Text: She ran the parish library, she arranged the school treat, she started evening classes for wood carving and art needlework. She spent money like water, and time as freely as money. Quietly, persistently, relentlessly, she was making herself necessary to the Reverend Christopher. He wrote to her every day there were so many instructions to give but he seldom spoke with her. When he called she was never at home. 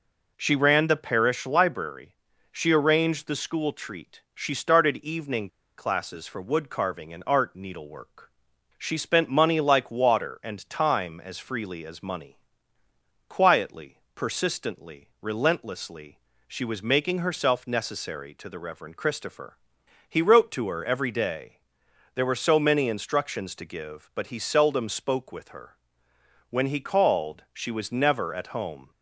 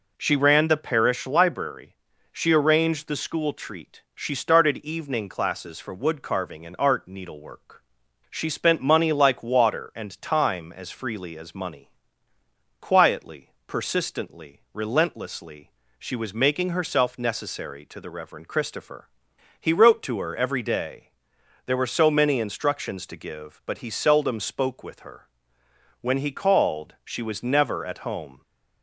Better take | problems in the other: second | pauses between "evening" and "classes"; slight; at 5.4 s; 0.29 s long // pauses between "day" and "there"; noticeable; at 21.5 s; 0.56 s long; noticeable in the second

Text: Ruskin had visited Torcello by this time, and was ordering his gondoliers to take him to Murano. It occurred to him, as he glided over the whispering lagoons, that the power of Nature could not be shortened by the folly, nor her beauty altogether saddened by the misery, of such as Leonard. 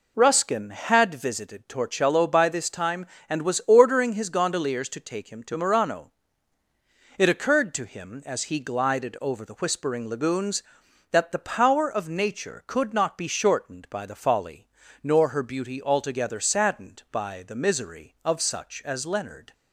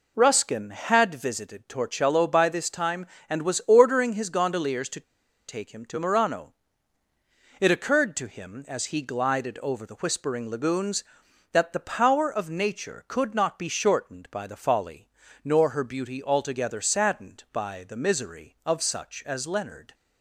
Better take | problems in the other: first | pauses between "to" and "take"; noticeable; at 4.9 s; 0.47 s long

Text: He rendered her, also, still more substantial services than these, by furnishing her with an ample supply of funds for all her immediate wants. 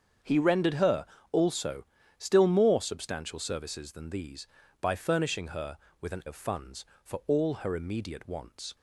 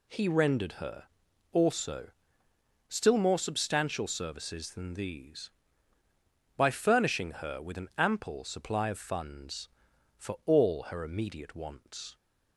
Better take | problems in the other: second | starts louder than the rest; strong; until 1.5 s; 7.5 dB // skips "ample supply"; at 6.2 s

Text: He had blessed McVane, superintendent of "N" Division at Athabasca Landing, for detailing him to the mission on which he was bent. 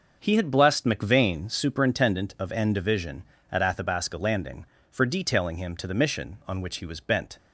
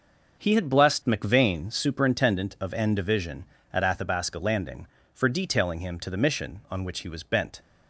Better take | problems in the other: neither | starts louder than the rest; noticeable; the same in both

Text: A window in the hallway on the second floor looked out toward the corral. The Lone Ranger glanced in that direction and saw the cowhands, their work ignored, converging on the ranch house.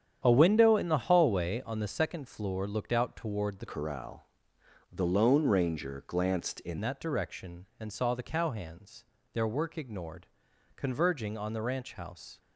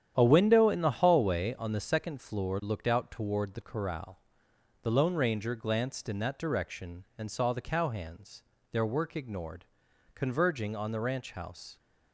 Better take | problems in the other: second | starts louder than the rest; strong; until 1.2 s; 9 dB; strong in the second // changes voice from "corral" to "in"; from 3.6 to 6.7 s; 3.1 s long

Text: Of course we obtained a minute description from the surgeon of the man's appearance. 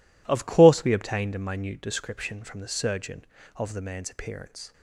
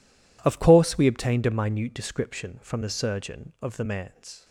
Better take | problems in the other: first | stops before "appearance"; at 4.4 s

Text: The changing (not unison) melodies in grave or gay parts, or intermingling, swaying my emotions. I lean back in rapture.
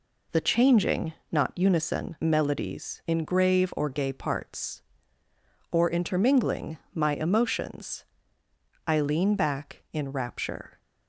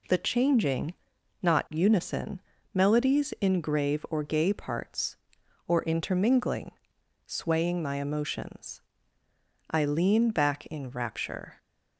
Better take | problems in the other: second | skips "swaying"; at 6.8 s

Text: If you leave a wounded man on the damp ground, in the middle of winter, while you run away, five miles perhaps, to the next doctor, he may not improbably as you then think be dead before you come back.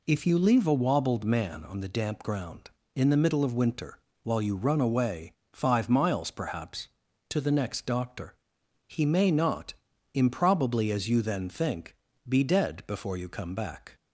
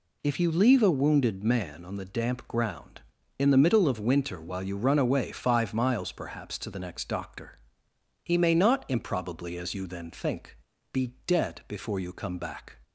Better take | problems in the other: second | says "wobbled" for "wounded"; at 0.7 s // pauses between "not" and "improbably"; at 9.7 s; 0.38 s long // pauses between "think" and "be"; slight; at 11.9 s; 0.34 s long; slight in the second

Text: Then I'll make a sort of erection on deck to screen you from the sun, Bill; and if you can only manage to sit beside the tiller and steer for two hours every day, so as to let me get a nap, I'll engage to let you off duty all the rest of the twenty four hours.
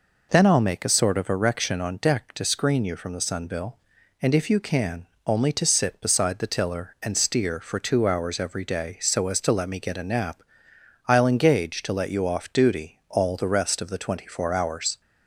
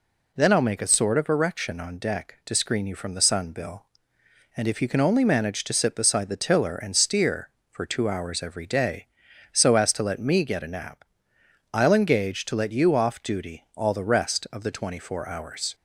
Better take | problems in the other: second | pauses between "can" and "only"; slight; at 5.0 s; 0.20 s long // skips "manage"; at 5.5 s

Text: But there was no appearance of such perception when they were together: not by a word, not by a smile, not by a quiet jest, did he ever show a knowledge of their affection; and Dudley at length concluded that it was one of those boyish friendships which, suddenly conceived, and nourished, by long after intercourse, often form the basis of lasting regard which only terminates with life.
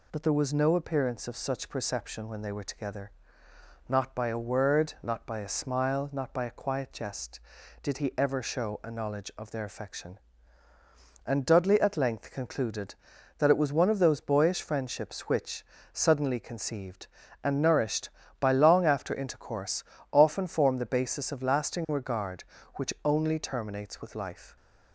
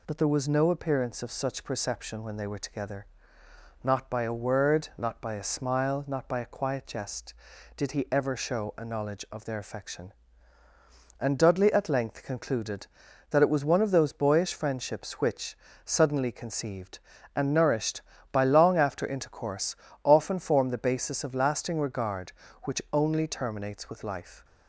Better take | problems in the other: neither | none

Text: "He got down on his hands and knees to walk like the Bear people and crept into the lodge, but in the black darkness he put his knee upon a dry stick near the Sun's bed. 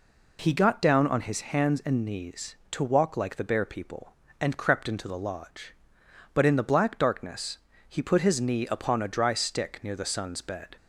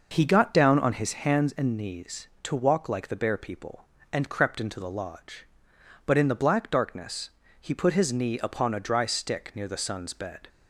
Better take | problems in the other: first | starts louder than the rest; noticeable; until 1.5 s; 5.5 dB // pauses between "darkness" and "he"; slight; at 7.2 s; 0.32 s long; slight in the first

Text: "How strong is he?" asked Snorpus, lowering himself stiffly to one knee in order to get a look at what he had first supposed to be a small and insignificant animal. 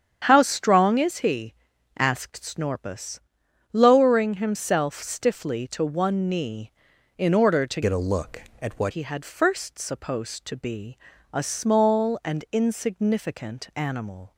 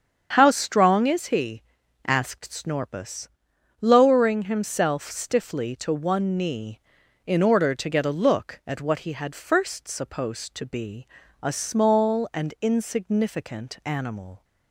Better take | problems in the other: second | starts louder than the rest; strong; until 1.2 s; 8.5 dB; strong in the second // changes voice from "get" to "what"; from 7.8 to 8.9 s; 1.1 s long // pauses between "be" and "a"; slight; at 10.9 s; 0.34 s long; slight in the second

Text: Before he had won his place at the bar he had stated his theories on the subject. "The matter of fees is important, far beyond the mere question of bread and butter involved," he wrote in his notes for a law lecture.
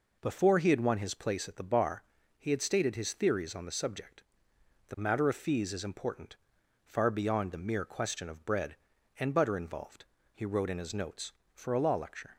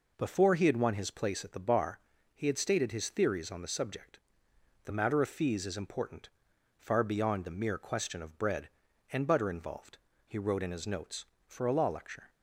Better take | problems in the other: neither | pauses between "bar" and "he"; the same in both

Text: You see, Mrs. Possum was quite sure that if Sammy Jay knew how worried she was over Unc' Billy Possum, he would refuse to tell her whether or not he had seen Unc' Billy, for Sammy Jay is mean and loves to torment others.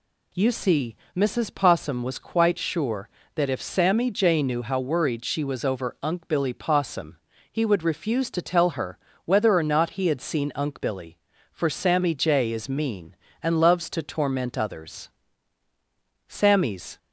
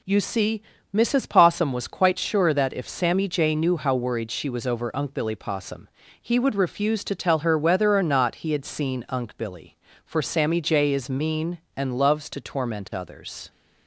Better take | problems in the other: second | pauses between "her" and "whether"; slight; at 8.9 s; 0.28 s long // goes on to say "Sammy's"; noticeable; from 16.2 s on; 0.70 s long

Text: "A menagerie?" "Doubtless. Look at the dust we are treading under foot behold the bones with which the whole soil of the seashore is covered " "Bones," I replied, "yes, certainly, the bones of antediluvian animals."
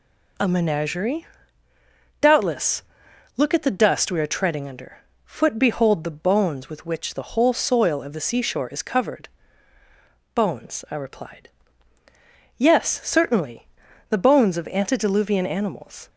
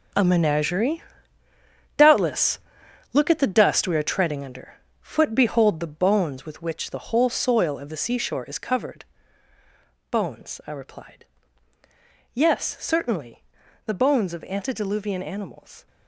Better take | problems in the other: first | gets quieter; strong; throughout; 13 dB // pauses between "under" and "foot"; slight; at 4.7 s; 0.26 s long; slight in the first

